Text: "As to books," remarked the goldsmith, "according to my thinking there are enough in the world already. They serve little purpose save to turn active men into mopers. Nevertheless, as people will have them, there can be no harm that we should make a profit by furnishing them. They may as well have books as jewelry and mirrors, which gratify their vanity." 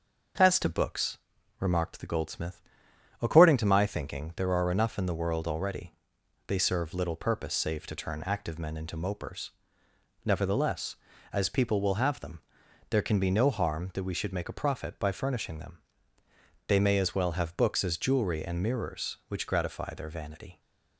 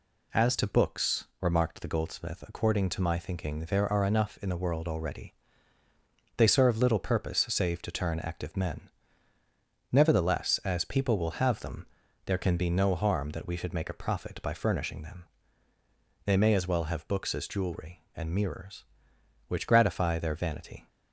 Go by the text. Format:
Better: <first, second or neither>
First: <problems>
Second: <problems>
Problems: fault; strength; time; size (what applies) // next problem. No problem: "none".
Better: first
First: none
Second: skips "into mopers"; at 9.4 s